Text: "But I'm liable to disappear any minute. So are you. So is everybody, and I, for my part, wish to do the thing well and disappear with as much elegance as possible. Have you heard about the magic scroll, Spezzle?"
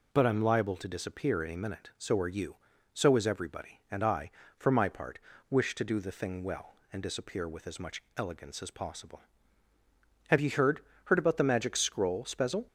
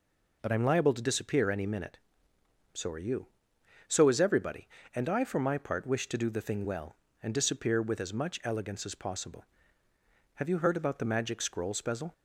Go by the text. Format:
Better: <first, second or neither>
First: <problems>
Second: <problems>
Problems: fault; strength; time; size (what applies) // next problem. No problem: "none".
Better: second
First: says "heard" twice; at 11.0 s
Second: none